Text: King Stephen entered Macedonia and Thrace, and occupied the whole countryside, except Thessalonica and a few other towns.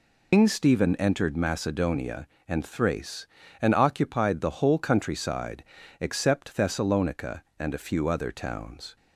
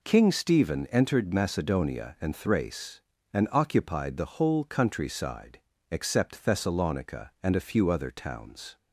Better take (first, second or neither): second